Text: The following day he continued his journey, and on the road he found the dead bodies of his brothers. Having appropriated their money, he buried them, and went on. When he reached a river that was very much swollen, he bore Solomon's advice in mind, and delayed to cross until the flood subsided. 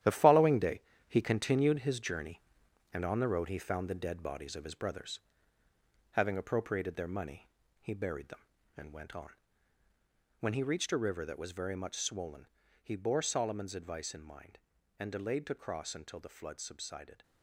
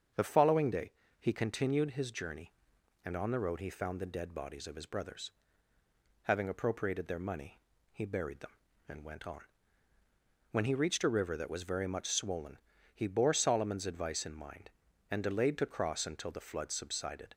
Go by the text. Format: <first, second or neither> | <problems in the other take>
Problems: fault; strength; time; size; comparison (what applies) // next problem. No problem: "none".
second | gets quieter; strong; throughout; 9.5 dB // starts louder than the rest; strong; until 1.3 s; 11.5 dB; strong in the second // pauses between "day" and "he"; slight; at 0.8 s; 0.27 s long; slight in the second